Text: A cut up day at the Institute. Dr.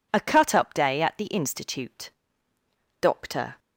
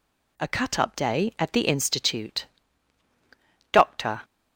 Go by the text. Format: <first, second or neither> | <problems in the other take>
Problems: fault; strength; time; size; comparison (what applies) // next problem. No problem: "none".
neither | none